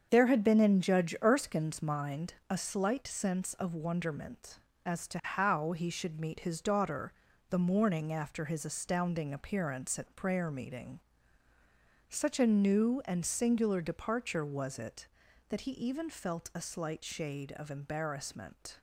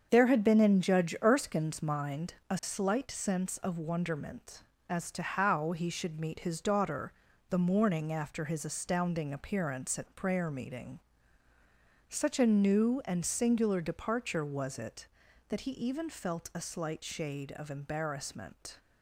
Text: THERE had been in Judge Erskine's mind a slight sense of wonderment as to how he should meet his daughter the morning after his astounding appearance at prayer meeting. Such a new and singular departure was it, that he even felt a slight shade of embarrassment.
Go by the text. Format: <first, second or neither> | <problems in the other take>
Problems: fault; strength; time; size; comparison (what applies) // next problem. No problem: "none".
neither | starts louder than the rest; the same in both // pauses between "mind" and "a"; slight; the same in both // pauses between "daughter" and "the"; slight; the same in both